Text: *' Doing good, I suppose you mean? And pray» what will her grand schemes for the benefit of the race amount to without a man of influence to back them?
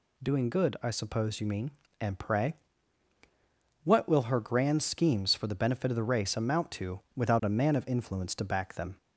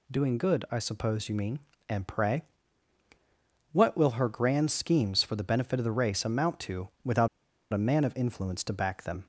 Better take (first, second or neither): first